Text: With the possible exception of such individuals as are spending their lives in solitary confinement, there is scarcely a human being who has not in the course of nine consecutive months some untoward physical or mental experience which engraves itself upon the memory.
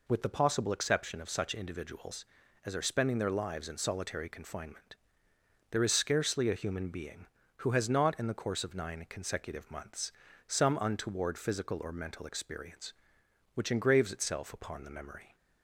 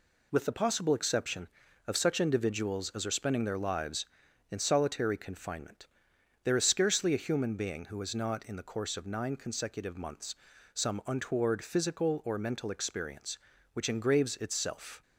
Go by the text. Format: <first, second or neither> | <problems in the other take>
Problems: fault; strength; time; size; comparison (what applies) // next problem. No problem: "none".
first | pauses between "months" and "some"; at 10.3 s; 0.40 s long; slight in the first // stops before "upon the memory"; at 15.0 s